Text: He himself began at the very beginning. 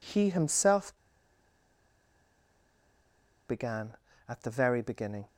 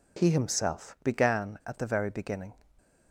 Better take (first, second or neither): second